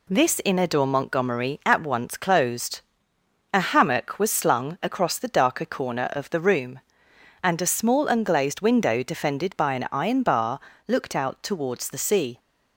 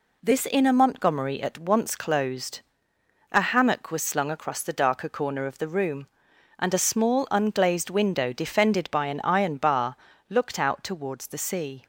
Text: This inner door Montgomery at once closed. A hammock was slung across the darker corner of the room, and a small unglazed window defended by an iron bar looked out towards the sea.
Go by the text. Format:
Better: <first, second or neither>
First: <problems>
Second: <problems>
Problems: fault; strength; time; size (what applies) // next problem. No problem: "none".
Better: first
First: pauses between "bar" and "looked"; slight; at 10.6 s; 0.26 s long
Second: skips "door"; at 0.7 s // pauses between "bar" and "looked"; slight; at 9.9 s; 0.32 s long